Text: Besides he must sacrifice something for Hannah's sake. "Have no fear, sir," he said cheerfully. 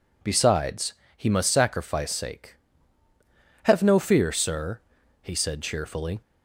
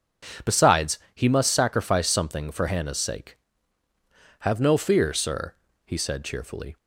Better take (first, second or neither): second